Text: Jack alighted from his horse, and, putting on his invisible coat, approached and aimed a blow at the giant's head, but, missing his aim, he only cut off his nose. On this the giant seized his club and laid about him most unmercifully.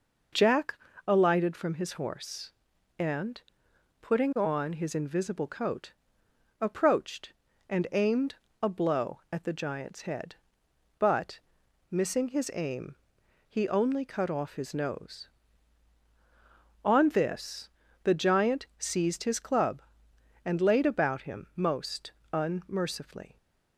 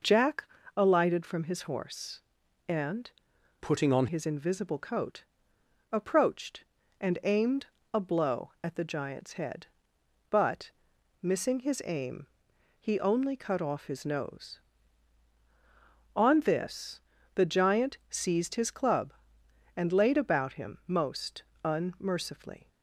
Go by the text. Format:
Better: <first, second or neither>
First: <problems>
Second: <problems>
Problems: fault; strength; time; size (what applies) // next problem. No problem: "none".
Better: first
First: pauses between "Jack" and "alighted"; slight; at 0.7 s; 0.32 s long // pauses between "aimed" and "a"; slight; at 8.3 s; 0.28 s long // pauses between "this" and "the"; slight; at 17.6 s; 0.36 s long // pauses between "most" and "unmercifully"; slight; at 22.1 s; 0.20 s long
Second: pauses between "Jack" and "alighted"; slight; at 0.4 s; 0.32 s long // changes voice from "putting" to "on"; from 3.6 to 4.0 s; 0.4 s long // pauses between "aimed" and "a"; slight; at 7.6 s; 0.28 s long // pauses between "this" and "the"; slight; at 16.9 s; 0.36 s long // pauses between "most" and "unmercifully"; slight; at 21.4 s; 0.20 s long